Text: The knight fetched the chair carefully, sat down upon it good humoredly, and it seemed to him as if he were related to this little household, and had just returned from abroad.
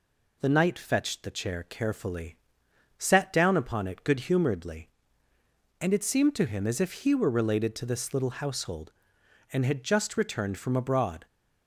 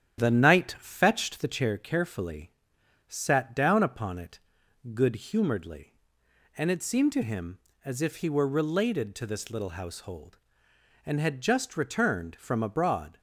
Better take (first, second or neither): first